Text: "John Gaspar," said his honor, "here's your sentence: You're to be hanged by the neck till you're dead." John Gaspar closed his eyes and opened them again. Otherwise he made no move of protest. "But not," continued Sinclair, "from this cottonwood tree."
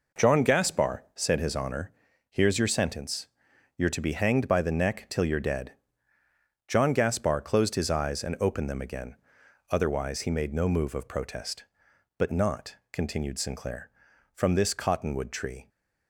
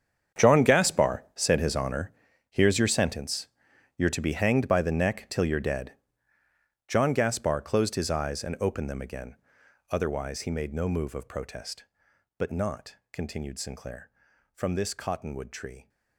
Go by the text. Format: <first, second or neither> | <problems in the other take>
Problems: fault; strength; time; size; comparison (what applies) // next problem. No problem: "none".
first | gets quieter; strong; throughout; 15 dB